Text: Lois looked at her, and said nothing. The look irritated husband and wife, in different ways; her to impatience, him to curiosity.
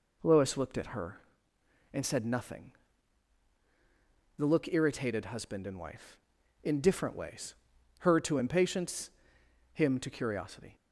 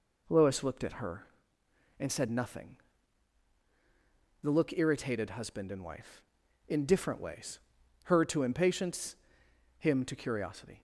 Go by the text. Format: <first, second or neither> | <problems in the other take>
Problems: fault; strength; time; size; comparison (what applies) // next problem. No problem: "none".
neither | none